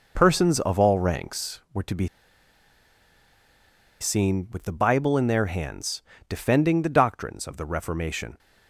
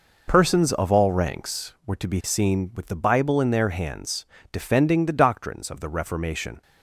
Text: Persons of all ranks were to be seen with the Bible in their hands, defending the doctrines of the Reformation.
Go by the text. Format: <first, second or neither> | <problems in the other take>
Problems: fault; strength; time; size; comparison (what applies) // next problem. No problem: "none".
second | pauses between "be" and "seen"; strong; at 2.0 s; 1.9 s long